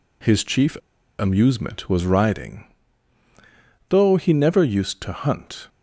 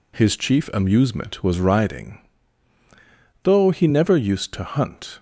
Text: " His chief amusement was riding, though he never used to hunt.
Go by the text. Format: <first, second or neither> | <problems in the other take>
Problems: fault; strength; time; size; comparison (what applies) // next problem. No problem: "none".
second | pauses between "chief" and "amusement"; at 0.7 s; 0.43 s long